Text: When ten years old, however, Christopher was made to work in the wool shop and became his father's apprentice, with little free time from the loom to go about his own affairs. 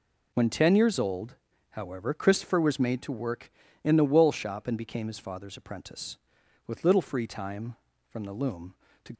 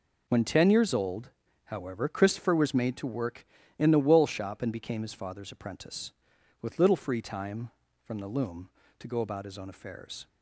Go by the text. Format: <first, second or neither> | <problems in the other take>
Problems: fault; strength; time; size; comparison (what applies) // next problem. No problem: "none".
second | stops before "go about his own affairs"; at 9.1 s